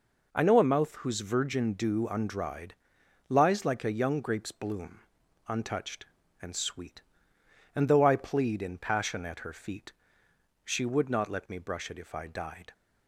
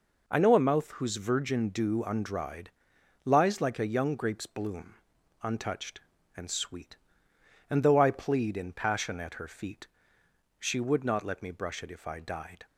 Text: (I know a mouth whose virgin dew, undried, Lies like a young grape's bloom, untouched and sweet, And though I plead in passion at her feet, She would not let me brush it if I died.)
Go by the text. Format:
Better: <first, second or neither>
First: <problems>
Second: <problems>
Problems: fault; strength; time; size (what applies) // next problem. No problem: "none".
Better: neither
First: none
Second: none